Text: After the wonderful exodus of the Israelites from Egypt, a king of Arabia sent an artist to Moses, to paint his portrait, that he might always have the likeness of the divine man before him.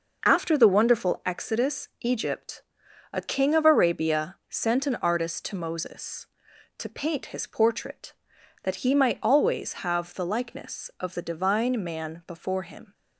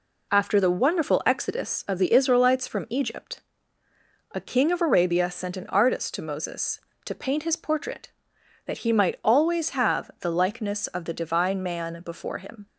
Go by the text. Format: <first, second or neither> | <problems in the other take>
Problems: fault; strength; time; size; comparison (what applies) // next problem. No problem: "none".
second | skips "of the Israelites from"; at 1.9 s